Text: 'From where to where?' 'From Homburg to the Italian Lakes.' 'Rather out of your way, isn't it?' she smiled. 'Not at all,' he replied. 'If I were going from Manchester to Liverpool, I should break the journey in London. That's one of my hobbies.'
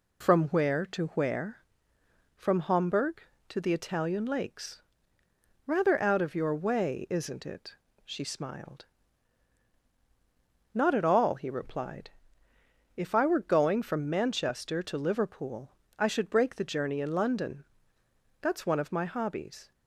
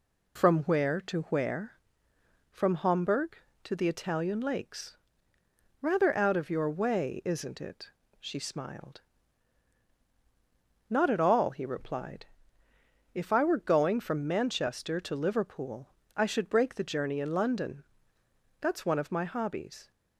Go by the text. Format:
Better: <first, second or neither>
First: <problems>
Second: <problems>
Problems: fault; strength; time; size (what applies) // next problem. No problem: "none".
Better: neither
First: none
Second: none